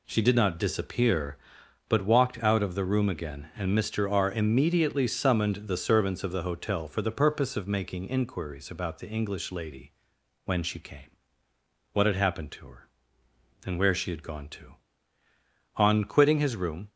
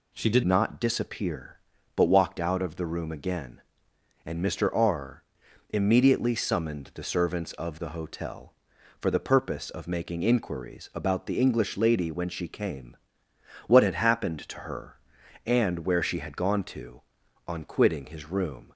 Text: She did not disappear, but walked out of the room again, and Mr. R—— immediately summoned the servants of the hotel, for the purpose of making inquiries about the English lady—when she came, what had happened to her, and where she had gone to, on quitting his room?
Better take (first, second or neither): first